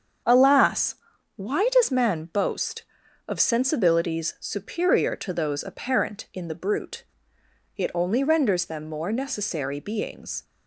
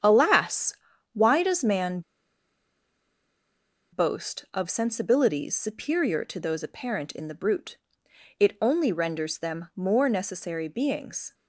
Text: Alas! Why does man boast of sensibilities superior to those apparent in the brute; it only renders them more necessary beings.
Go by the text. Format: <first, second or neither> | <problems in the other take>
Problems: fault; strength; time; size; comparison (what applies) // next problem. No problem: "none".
first | starts louder than the rest; strong; until 1.4 s; 9 dB; strong in the first // pauses between "man" and "boast"; strong; at 2.0 s; 1.9 s long